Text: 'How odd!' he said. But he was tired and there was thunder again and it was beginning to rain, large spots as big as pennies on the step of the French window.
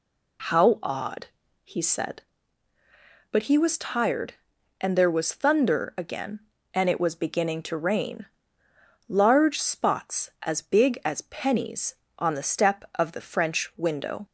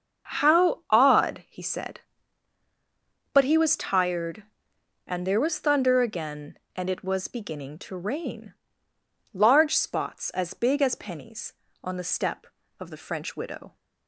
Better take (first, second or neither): first